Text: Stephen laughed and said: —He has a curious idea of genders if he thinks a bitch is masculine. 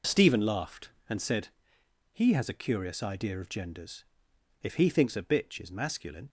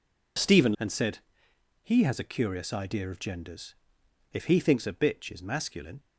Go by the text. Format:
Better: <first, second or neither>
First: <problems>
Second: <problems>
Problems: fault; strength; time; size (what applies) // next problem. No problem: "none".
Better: first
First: pauses between "genders" and "if"; noticeable; at 4.0 s; 0.58 s long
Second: skips "laughed"; at 0.7 s // pauses between "genders" and "if"; noticeable; at 3.7 s; 0.58 s long